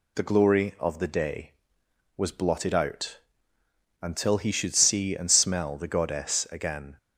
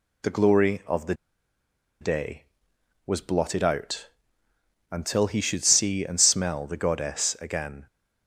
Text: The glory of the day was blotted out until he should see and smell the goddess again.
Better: first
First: pauses between "out" and "until"; noticeable; at 3.1 s; 0.82 s long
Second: pauses between "the" and "day"; noticeable; at 1.1 s; 0.86 s long // pauses between "out" and "until"; noticeable; at 4.0 s; 0.82 s long

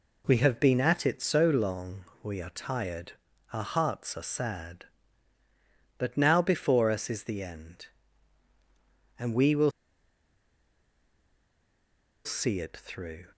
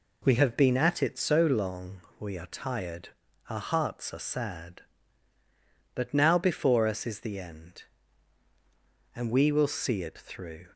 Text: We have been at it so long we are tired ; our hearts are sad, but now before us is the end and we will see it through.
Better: second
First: pauses between "long" and "we"; slight; at 2.0 s; 0.20 s long // pauses between "will" and "see"; strong; at 9.7 s; 2.5 s long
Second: pauses between "long" and "we"; slight; at 1.9 s; 0.20 s long

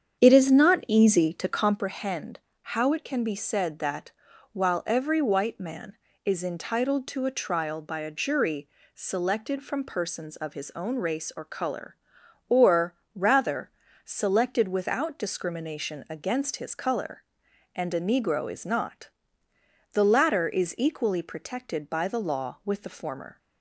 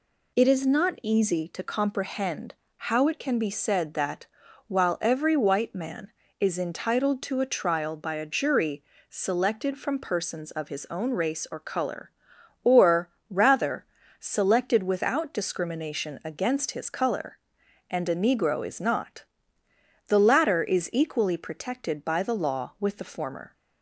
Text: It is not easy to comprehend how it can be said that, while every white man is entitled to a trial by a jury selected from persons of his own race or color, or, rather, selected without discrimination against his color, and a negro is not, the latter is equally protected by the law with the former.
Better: second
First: starts louder than the rest; strong; until 1.8 s; 8 dB // pauses between "comprehend" and "how"; slight; at 2.3 s; 0.30 s long // pauses between "jury" and "selected"; slight; at 8.6 s; 0.26 s long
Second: pauses between "comprehend" and "how"; slight; at 2.5 s; 0.30 s long // pauses between "jury" and "selected"; slight; at 8.8 s; 0.26 s long

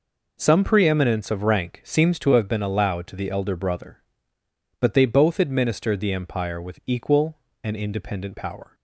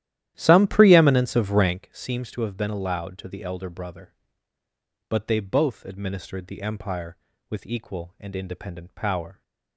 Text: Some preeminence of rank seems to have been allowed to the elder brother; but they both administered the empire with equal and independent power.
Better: first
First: none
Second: starts louder than the rest; strong; until 1.9 s; 12.5 dB

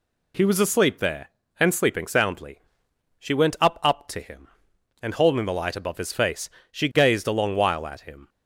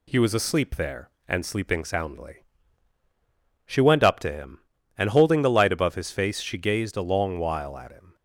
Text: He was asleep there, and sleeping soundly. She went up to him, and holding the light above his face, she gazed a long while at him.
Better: second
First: says "up" twice; at 3.8 s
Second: none

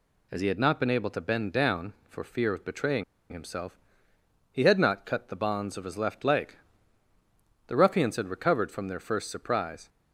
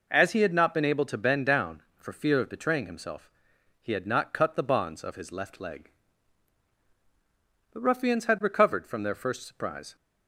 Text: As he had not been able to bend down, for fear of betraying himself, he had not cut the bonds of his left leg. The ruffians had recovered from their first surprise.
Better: second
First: pauses between "betraying" and "himself"; slight; at 3.0 s; 0.28 s long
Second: none

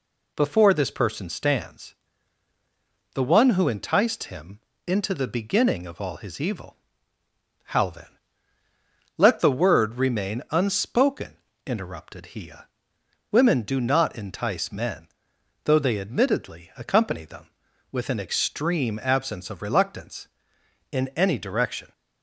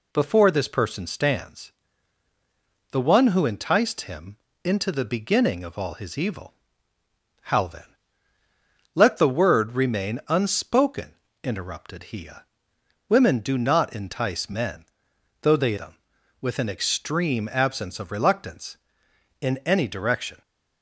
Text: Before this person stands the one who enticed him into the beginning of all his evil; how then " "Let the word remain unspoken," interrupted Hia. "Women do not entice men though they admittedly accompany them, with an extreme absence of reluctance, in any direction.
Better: first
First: pauses between "stands" and "the"; at 1.9 s; 1.2 s long // pauses between "him" and "into"; slight; at 4.5 s; 0.28 s long // pauses between "men" and "though"; noticeable; at 15.0 s; 0.58 s long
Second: pauses between "stands" and "the"; at 1.7 s; 1.2 s long // pauses between "him" and "into"; slight; at 4.3 s; 0.28 s long // pauses between "men" and "though"; noticeable; at 14.8 s; 0.58 s long // skips "admittedly accompany"; at 15.7 s

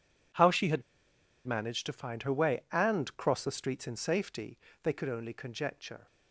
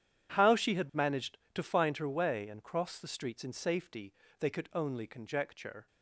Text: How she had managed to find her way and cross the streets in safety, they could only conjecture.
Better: second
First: pauses between "had" and "managed"; noticeable; at 0.8 s; 0.65 s long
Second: none

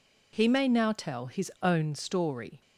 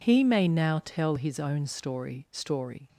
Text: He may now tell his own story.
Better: first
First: none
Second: says "story" twice; at 2.3 s

